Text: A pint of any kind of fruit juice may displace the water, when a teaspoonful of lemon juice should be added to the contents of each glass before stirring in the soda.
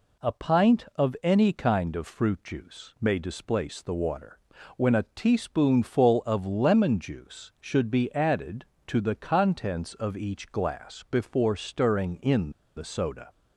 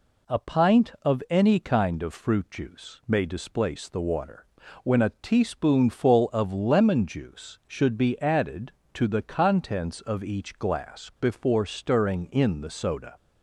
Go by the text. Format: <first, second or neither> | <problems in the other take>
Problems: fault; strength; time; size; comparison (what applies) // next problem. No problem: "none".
second | pauses between "in" and "the"; slight; at 12.4 s; 0.26 s long